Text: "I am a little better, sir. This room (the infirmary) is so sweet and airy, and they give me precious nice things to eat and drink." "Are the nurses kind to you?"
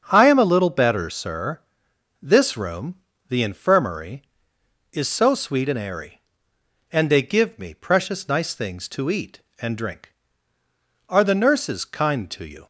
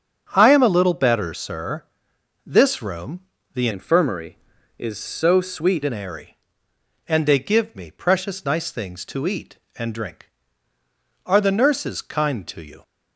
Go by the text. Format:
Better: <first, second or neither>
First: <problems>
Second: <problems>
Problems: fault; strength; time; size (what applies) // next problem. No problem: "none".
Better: first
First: starts louder than the rest; until 1.1 s; 7 dB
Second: starts louder than the rest; strong; until 1.3 s; 7.5 dB // changes voice from "infirmary" to "sweet"; from 3.7 to 5.8 s; 2.1 s long